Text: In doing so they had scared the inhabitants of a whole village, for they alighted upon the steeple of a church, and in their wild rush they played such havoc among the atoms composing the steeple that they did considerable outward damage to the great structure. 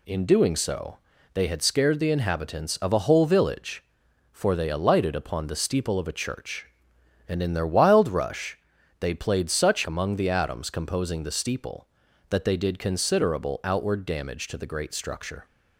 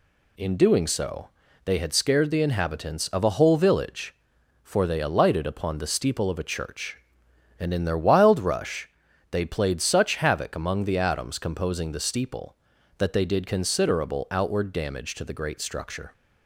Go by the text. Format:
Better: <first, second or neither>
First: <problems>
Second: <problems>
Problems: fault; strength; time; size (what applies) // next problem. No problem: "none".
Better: second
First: pauses between "so" and "they"; slight; at 0.9 s; 0.36 s long // pauses between "rush" and "they"; at 8.5 s; 0.40 s long // skips "havoc"; at 9.8 s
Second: pauses between "so" and "they"; slight; at 1.2 s; 0.36 s long // pauses between "rush" and "they"; at 8.8 s; 0.40 s long